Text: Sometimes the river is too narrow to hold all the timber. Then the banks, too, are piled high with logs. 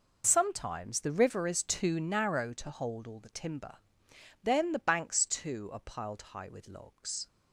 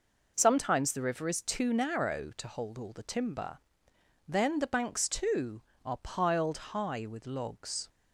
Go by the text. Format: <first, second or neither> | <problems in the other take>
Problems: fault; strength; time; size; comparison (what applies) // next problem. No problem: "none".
neither | none